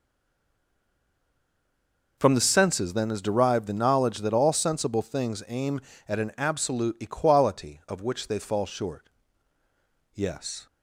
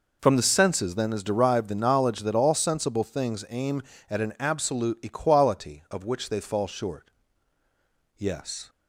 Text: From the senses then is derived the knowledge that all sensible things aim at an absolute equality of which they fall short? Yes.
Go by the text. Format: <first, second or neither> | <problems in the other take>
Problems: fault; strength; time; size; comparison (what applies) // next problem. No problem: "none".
second | stays silent before the first word; until 2.1 s; 2.1 s long